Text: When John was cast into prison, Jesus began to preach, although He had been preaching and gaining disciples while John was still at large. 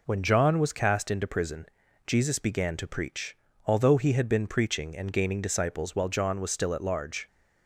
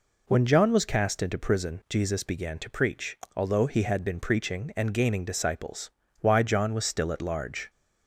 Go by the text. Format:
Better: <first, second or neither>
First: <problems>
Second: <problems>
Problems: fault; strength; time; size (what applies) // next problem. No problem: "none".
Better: first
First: none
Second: says "why" for "while"; at 6.1 s